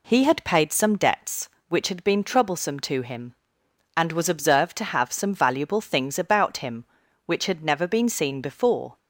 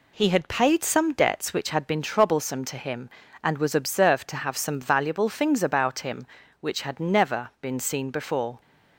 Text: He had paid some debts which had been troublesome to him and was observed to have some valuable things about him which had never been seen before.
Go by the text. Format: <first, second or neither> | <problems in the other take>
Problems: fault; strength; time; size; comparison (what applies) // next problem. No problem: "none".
neither | none